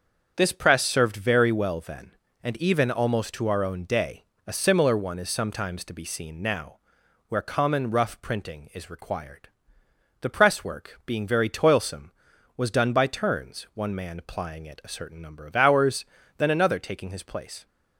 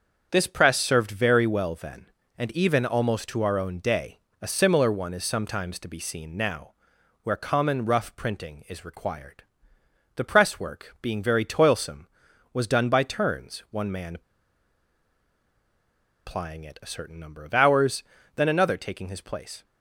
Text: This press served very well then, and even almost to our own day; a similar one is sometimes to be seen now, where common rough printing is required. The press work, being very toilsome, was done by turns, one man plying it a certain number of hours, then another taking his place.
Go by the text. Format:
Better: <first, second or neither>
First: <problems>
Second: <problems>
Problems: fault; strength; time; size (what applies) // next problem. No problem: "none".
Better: first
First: starts louder than the rest; until 1.3 s; 7 dB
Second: starts louder than the rest; until 1.3 s; 7 dB // pauses between "man" and "plying"; strong; at 14.1 s; 2.0 s long